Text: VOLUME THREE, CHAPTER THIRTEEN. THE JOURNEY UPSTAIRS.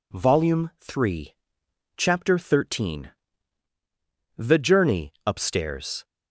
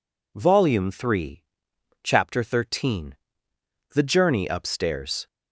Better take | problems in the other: neither | none

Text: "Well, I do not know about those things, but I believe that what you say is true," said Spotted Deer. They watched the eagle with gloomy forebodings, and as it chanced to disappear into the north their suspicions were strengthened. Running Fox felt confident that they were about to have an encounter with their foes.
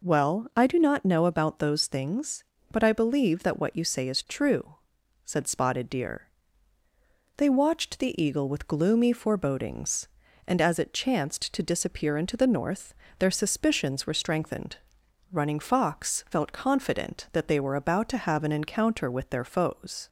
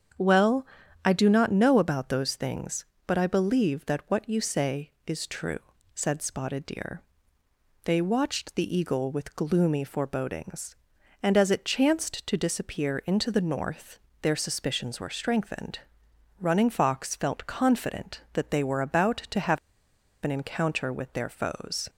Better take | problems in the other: first | starts louder than the rest; strong; until 1.5 s; 7.5 dB // pauses between "north" and "their"; slight; at 13.9 s; 0.22 s long; slight in the first // pauses between "have" and "an"; noticeable; at 19.5 s; 0.67 s long

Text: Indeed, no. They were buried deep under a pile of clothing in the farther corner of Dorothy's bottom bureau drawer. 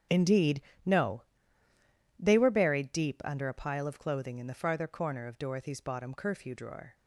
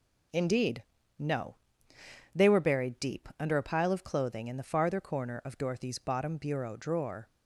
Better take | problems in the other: second | starts louder than the rest; strong; until 2.3 s; 8.5 dB // says "curfew" for "bureau"; at 6.1 s

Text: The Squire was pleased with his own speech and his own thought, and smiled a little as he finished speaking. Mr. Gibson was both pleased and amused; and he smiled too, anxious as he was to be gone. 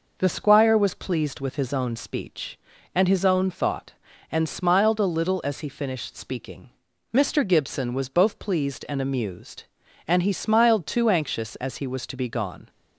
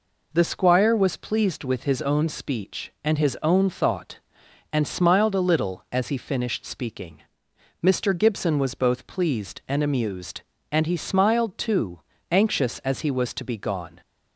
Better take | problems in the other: neither | none

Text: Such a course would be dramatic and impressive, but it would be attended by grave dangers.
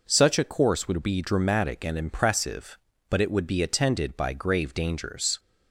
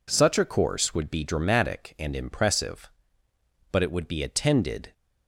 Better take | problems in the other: first | stops before "by grave dangers"; at 4.9 s

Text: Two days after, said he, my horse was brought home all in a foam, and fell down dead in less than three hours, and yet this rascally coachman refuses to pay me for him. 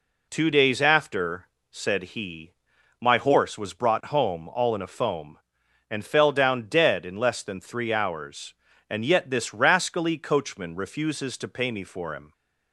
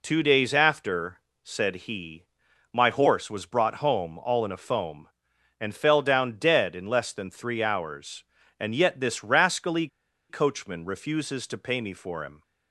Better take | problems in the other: first | pauses between "rascally" and "coachman"; at 9.8 s; 0.41 s long

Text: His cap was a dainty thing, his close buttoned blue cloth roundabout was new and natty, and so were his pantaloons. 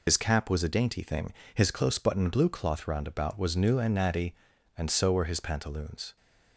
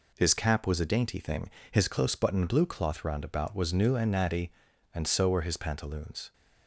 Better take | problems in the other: second | loses the start of "His"; at 0.0 s; 95 ms

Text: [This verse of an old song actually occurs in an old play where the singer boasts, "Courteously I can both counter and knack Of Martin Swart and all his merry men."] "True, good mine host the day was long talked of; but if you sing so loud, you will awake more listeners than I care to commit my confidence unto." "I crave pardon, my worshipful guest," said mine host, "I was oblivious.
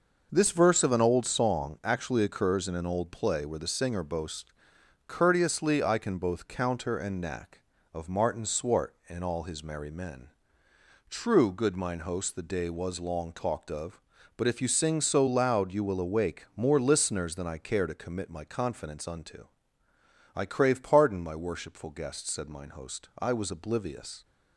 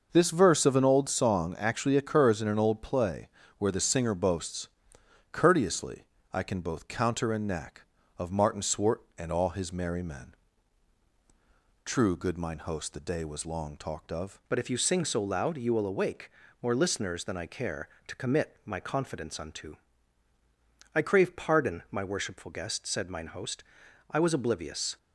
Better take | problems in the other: first | pauses between "play" and "where"; slight; at 3.2 s; 0.32 s long // pauses between "Courteously" and "I"; slight; at 6.0 s; 0.28 s long // changes voice at "but"; from 14.4 s on; 10.5 s long // pauses between "awake" and "more"; slight; at 16.2 s; 0.32 s long

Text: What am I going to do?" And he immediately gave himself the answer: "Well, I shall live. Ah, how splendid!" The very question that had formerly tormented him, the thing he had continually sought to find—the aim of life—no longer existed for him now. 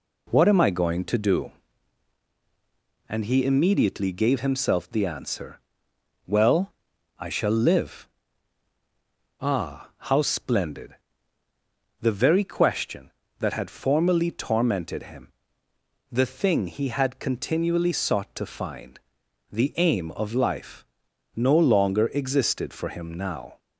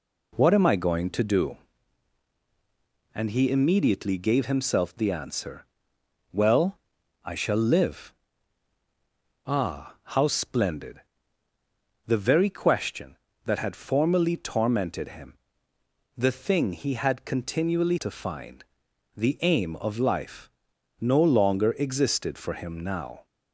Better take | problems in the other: first | skips "sought"; at 17.9 s

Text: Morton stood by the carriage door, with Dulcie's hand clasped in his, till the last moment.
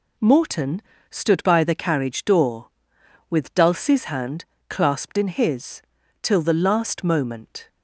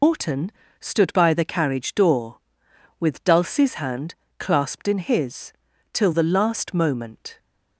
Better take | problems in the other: first | loses the start of "Morton"; at 0.0 s; 135 ms // pauses between "Morton" and "stood"; slight; at 0.5 s; 0.30 s long; slight in the first // pauses between "hand" and "clasped"; slight; at 4.1 s; 0.22 s long; slight in the first

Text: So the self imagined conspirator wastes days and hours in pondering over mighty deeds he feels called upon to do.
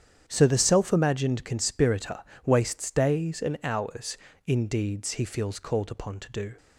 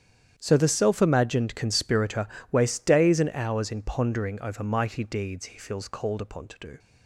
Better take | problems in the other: second | starts louder than the rest; strong; until 1.2 s; 9 dB; strong in the second // pauses between "conspirator" and "wastes"; slight; at 2.2 s; 0.24 s long; slight in the second // skips "pondering over mighty"; at 4.6 s

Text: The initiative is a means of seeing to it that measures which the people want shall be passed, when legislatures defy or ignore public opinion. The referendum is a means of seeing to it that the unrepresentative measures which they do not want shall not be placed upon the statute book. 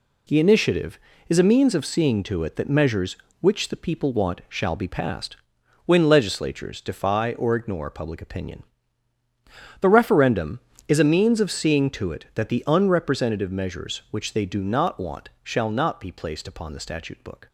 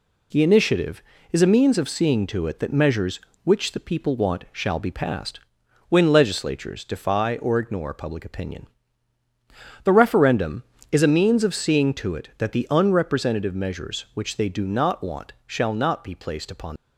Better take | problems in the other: first | stops before "the statute book"; at 16.7 s

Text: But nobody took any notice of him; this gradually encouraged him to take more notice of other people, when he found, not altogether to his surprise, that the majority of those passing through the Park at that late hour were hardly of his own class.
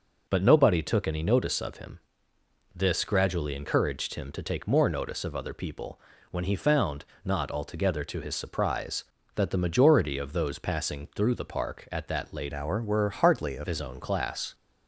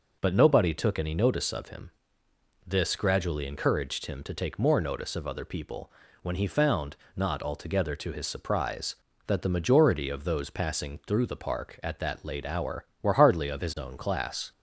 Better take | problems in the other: second | changes voice from "hour" to "of"; from 12.5 to 13.6 s; 1.1 s long

